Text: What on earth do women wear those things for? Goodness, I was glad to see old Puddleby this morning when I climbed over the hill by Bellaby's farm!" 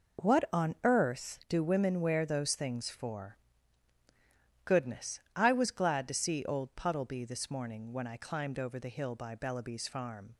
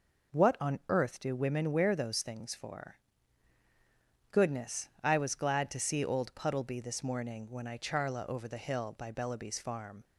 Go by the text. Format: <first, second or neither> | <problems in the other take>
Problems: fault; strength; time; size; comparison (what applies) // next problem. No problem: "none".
first | says "charla" for "climbed"; at 7.7 s